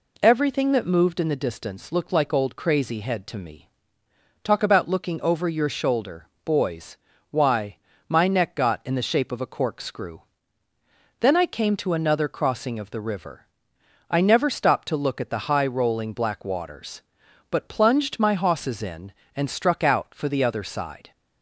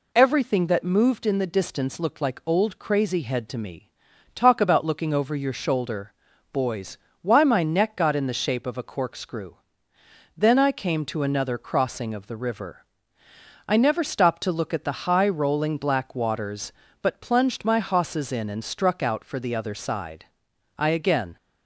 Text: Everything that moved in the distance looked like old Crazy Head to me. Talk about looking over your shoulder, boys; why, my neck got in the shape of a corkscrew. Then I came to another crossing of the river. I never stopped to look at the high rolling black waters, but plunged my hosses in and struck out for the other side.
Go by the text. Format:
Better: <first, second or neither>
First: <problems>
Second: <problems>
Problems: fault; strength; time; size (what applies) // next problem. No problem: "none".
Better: first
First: none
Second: goes on to say "I again"; from 20.7 s on; 0.60 s long